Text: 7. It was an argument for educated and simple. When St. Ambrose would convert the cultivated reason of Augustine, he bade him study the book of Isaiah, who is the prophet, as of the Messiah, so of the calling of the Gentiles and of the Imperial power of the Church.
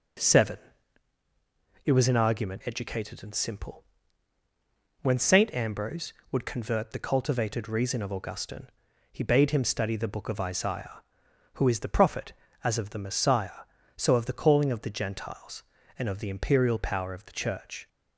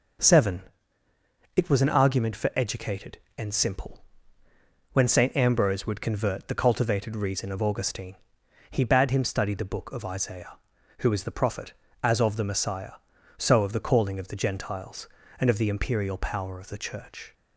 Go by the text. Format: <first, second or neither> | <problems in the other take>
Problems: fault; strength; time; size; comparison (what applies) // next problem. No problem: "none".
second | starts louder than the rest; until 2.4 s; 6.5 dB // skips "for"; at 2.6 s